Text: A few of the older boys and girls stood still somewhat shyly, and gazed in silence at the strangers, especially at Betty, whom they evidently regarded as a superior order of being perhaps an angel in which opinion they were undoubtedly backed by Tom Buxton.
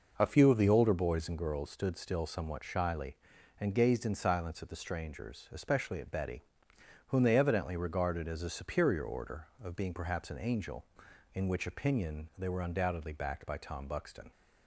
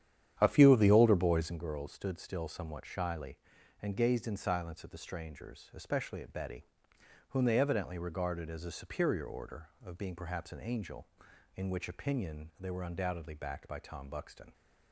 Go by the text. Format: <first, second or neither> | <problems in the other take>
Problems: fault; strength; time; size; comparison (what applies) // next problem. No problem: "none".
first | starts louder than the rest; strong; until 1.5 s; 10 dB